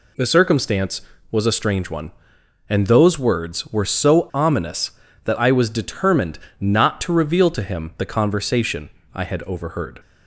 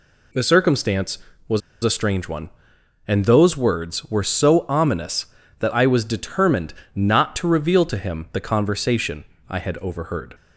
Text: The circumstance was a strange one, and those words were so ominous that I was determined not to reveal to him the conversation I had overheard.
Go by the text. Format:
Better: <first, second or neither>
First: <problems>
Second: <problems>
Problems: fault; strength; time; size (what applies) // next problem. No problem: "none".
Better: first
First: pauses between "determined" and "not"; slight; at 6.3 s; 0.22 s long // pauses between "conversation" and "I"; slight; at 8.8 s; 0.24 s long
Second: pauses between "was" and "a"; slight; at 1.6 s; 0.22 s long // pauses between "determined" and "not"; slight; at 6.7 s; 0.22 s long // pauses between "conversation" and "I"; slight; at 9.2 s; 0.24 s long